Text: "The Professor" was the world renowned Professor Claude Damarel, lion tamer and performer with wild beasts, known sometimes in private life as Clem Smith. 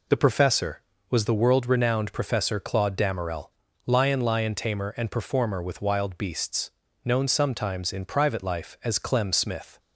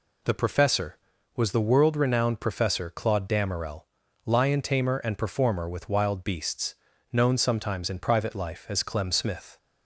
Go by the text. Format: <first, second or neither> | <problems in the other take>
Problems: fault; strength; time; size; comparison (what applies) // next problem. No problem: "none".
second | says "lion" twice; at 4.2 s